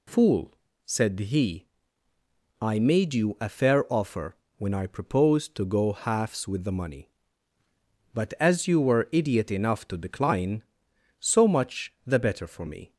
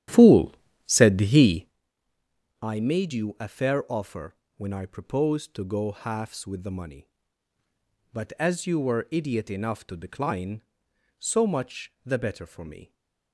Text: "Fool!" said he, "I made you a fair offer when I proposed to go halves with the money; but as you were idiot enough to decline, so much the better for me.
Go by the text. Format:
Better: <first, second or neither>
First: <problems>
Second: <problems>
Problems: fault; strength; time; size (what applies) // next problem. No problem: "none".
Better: first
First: pauses between "offer" and "when"; slight; at 4.3 s; 0.20 s long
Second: starts louder than the rest; strong; until 1.8 s; 11.5 dB // pauses between "offer" and "when"; slight; at 4.3 s; 0.20 s long